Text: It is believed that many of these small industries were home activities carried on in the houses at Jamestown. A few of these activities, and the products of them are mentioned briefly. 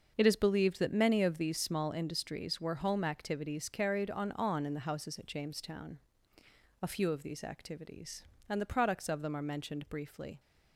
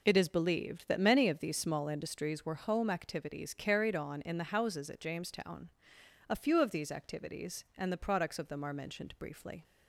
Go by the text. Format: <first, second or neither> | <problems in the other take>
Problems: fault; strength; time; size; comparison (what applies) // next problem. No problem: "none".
second | starts louder than the rest; noticeable; until 1.2 s; 6 dB // says "on" twice; at 4.3 s